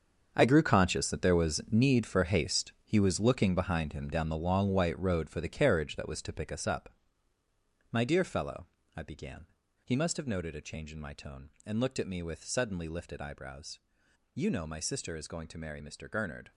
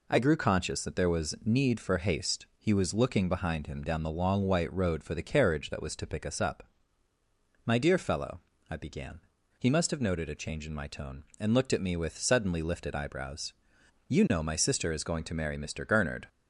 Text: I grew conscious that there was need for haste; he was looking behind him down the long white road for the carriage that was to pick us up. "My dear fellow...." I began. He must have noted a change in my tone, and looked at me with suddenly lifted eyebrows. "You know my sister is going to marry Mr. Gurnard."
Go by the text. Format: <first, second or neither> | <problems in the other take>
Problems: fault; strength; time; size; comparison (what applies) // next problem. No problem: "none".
second | gets quieter; strong; throughout; 12.5 dB